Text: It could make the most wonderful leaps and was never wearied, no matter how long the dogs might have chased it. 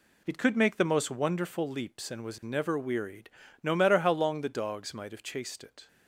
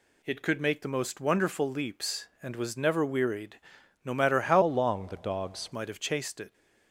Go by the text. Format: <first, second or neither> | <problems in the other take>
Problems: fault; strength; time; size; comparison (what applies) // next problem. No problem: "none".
first | changes voice from "long" to "dogs"; from 4.6 to 5.7 s; 1.1 s long